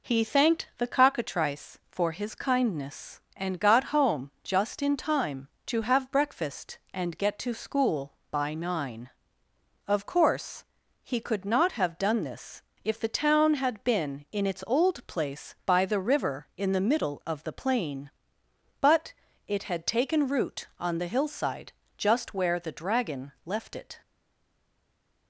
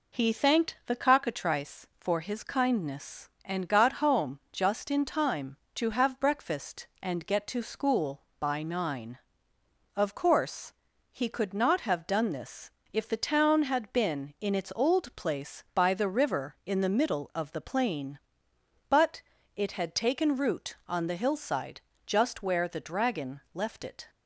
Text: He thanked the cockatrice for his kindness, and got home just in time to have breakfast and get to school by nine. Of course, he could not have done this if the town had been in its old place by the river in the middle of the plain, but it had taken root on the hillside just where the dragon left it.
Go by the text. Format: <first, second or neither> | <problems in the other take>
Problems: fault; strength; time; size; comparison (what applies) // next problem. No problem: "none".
second | pauses between "this" and "if"; slight; at 12.6 s; 0.22 s long; slight in the second // pauses between "but" and "it"; slight; at 19.1 s; 0.36 s long; slight in the second // pauses between "hillside" and "just"; slight; at 21.7 s; 0.24 s long; slight in the second // stays silent after the last word; noticeable; from 24.0 s on; 1.2 s long